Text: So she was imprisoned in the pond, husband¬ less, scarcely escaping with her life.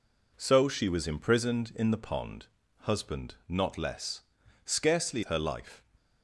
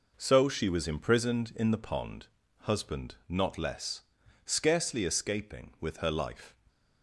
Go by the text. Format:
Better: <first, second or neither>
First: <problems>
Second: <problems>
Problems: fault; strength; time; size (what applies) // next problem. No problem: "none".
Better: second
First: skips "escaping with"; at 5.2 s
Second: none